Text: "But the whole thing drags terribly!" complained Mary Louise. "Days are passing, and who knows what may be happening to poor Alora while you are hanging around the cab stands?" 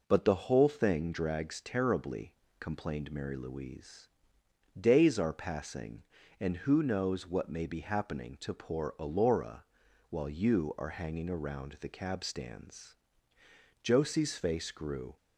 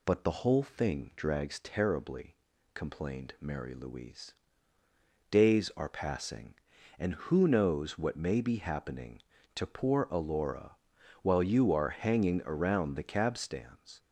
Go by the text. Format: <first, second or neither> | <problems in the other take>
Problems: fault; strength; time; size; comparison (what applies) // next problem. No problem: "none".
second | pauses between "Alora" and "while"; noticeable; at 9.6 s; 0.46 s long; noticeable in the second // goes on to say "Josie's face grew"; from 13.8 s on; 1.3 s long